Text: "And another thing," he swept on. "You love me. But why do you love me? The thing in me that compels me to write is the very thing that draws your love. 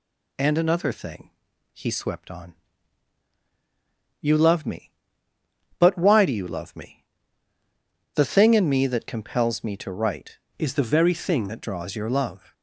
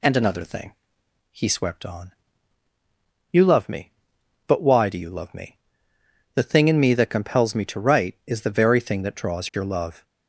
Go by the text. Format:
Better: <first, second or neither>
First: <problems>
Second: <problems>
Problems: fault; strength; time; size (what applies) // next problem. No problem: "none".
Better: second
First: changes voice from "is" to "thing"; from 10.5 to 11.4 s; 0.9 s long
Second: none